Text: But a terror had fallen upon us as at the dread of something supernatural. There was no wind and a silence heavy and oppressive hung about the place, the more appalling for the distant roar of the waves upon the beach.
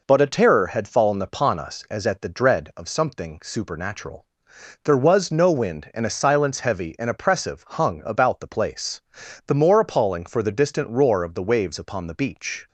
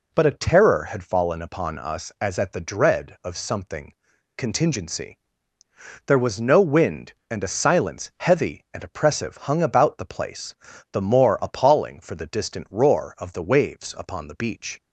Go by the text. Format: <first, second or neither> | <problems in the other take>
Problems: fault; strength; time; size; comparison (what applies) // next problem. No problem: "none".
first | says "contingency" for "supernatural"; at 4.3 s